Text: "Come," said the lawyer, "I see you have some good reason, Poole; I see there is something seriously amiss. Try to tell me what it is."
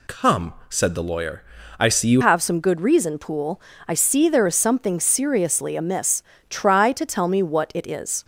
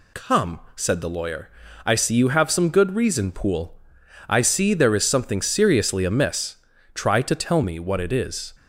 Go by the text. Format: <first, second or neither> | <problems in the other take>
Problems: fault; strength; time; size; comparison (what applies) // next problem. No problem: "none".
second | changes voice at "have"; from 2.2 s on; 6.0 s long